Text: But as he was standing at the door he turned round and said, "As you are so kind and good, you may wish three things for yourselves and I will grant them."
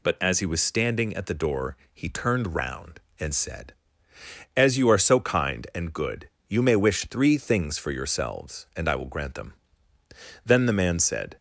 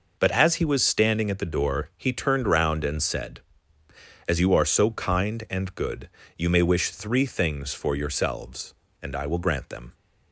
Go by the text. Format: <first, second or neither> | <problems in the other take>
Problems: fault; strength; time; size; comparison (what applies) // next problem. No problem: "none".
second | pauses between "door" and "he"; slight; at 1.7 s; 0.16 s long // goes on to say "Then the man said"; noticeable; from 10.4 s on; 0.92 s long